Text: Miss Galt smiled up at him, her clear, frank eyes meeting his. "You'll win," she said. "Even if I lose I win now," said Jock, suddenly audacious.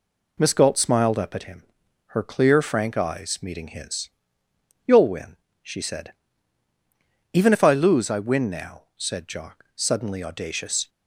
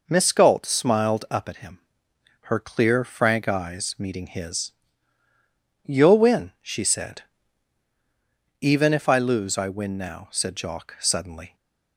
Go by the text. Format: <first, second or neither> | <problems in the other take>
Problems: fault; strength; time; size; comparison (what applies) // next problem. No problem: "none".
first | stops before "audacious"; at 11.5 s